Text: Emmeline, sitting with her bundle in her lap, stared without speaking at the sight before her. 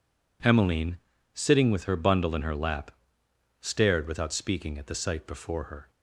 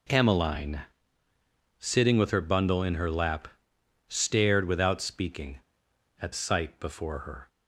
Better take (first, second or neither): first